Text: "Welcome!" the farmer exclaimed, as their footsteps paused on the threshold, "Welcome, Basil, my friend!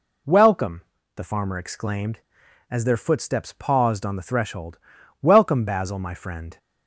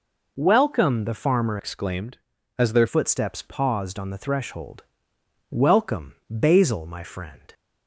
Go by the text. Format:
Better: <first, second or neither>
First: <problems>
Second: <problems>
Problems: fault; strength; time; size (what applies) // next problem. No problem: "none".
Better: first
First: none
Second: changes voice from "exclaimed" to "their"; from 1.5 to 2.8 s; 1.3 s long